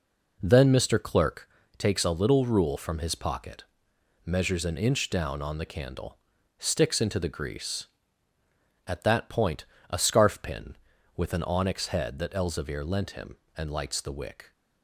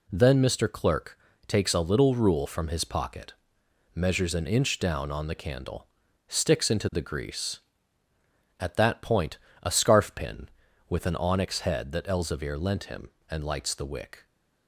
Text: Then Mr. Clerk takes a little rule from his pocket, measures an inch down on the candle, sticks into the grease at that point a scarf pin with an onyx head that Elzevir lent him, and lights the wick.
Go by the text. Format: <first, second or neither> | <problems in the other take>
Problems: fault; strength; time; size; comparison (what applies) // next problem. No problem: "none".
second | starts louder than the rest; noticeable; until 1.5 s; 4.5 dB // pauses between "Clerk" and "takes"; slight; at 1.4 s; 0.30 s long; slight in the second // pauses between "point" and "a"; slight; at 9.6 s; 0.24 s long; slight in the second